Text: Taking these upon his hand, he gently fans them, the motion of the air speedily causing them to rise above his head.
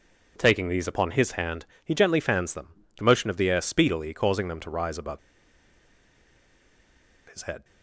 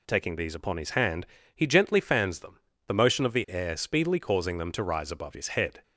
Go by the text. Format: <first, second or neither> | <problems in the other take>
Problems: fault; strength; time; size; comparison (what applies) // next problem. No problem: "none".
second | pauses between "above" and "his"; strong; at 5.1 s; 2.0 s long